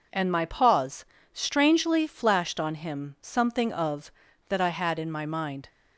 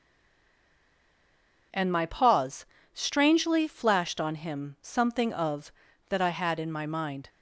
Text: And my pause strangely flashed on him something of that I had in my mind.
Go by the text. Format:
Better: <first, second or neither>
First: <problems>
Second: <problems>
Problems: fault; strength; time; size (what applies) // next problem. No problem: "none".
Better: first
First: pauses between "pause" and "strangely"; slight; at 1.0 s; 0.28 s long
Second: stays silent before the first word; noticeable; until 1.7 s; 1.7 s long // pauses between "pause" and "strangely"; slight; at 2.6 s; 0.28 s long